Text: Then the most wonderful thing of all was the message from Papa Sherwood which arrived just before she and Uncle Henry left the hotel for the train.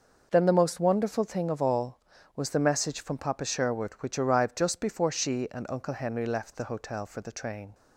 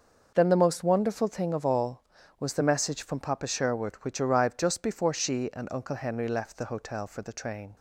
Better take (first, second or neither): neither